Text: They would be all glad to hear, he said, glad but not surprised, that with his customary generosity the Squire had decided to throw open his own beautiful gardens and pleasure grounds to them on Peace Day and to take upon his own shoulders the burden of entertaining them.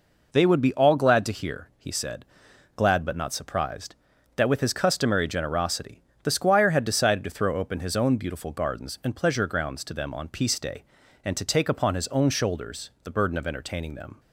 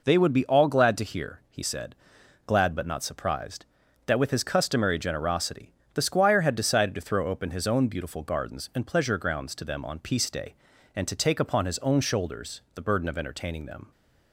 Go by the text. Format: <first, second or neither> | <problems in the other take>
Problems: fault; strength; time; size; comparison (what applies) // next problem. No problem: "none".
neither | pauses between "generosity" and "the"; slight; the same in both